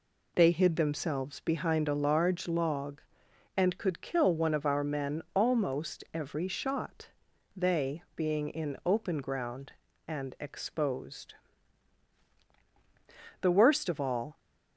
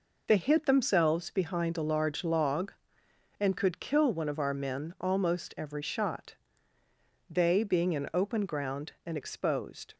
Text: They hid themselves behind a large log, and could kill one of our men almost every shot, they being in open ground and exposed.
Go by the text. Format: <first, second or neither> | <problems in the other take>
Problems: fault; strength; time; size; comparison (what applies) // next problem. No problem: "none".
second | goes on to say "The worst of all"; noticeable; from 13.3 s on; 0.98 s long